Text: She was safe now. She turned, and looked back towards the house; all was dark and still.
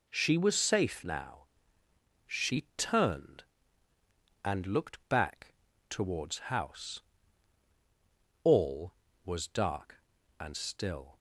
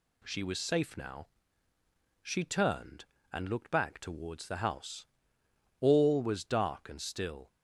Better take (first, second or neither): second